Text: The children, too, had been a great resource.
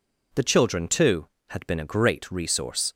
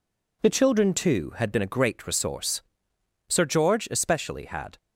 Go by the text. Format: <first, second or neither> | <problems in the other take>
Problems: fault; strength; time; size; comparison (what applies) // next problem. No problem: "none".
first | goes on to say "Sir George especially had"; from 3.2 s on; 1.4 s long